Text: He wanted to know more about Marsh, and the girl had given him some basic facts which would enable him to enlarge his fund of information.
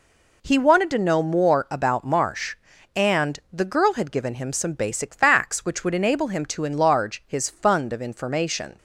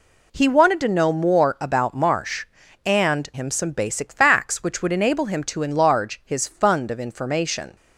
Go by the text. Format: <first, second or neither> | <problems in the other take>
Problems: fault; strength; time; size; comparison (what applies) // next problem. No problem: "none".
first | skips "the girl had given"; at 3.3 s